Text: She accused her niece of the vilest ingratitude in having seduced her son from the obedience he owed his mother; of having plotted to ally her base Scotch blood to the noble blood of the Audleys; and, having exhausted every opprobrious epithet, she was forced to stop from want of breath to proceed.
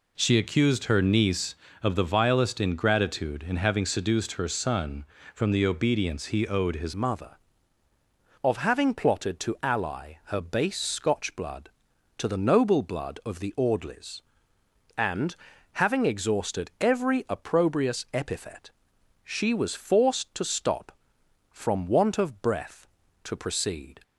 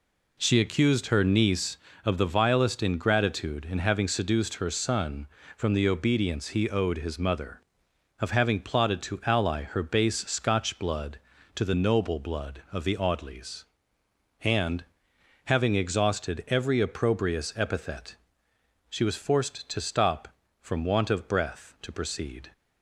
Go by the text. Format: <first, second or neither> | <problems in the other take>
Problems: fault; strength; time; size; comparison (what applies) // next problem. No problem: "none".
second | changes voice at "mother"; from 6.9 s on; 17.1 s long